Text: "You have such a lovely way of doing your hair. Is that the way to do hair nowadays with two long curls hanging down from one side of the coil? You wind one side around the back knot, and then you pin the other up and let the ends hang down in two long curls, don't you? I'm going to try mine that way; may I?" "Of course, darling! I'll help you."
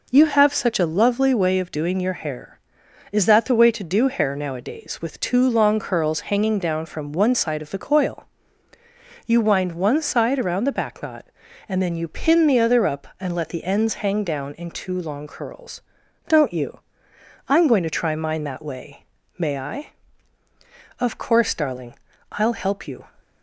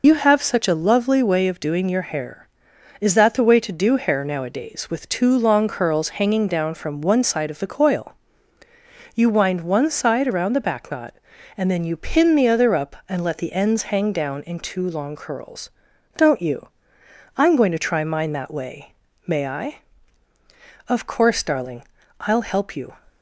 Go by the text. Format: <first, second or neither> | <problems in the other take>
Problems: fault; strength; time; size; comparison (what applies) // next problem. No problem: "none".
first | loses the start of "You"; at 0.0 s; 60 ms